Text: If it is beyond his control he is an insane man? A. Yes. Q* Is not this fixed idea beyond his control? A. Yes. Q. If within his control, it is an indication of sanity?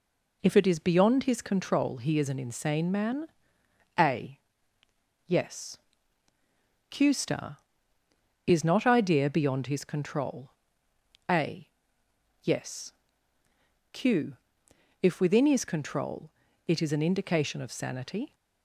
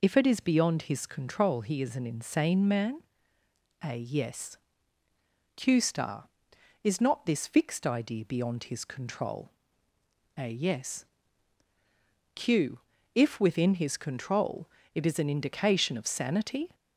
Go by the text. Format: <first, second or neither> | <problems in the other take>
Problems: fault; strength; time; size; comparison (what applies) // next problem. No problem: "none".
second | skips "this fixed"; at 8.8 s